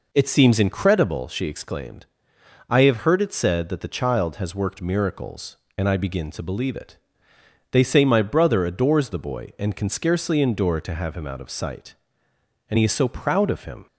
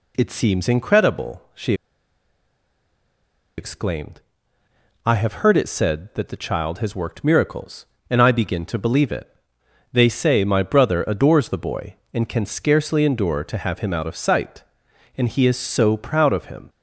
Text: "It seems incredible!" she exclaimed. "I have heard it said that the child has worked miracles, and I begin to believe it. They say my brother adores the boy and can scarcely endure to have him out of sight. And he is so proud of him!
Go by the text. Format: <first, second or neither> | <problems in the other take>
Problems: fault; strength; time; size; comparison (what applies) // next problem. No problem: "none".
first | pauses between "she" and "exclaimed"; strong; at 1.7 s; 1.8 s long